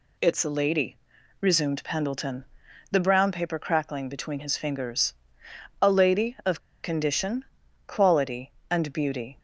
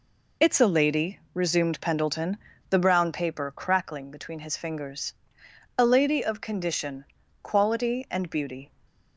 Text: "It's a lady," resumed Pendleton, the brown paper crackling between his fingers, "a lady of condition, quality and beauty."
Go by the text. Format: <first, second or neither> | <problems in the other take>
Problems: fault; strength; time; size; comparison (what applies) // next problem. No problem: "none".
second | pauses between "of" and "condition"; slight; at 6.5 s; 0.23 s long